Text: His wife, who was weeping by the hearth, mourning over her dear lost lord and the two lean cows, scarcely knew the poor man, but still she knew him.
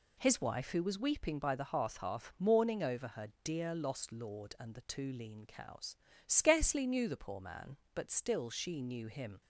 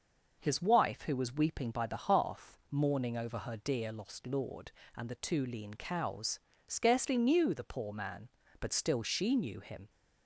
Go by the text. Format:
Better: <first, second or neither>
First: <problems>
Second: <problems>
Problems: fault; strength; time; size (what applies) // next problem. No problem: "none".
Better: second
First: says "hearth" twice; at 1.9 s // pauses between "her" and "dear"; slight; at 3.2 s; 0.16 s long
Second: none